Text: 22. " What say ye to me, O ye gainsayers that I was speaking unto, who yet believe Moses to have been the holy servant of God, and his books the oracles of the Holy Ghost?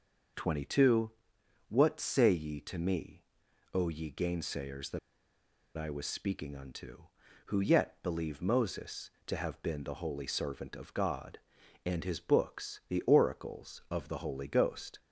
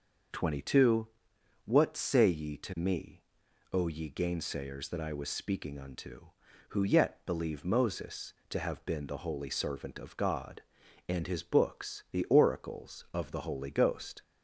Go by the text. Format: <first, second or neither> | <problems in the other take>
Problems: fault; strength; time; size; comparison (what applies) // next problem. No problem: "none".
second | pauses between "that" and "I"; noticeable; at 4.9 s; 0.78 s long